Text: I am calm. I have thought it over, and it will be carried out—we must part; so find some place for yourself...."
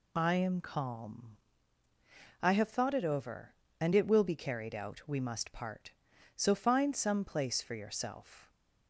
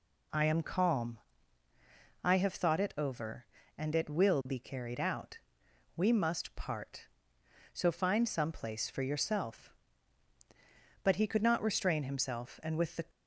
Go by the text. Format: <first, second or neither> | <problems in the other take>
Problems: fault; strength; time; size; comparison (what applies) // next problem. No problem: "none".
first | goes on to say "But he could not restrain himself and with the"; strong; from 11.0 s on; 2.0 s long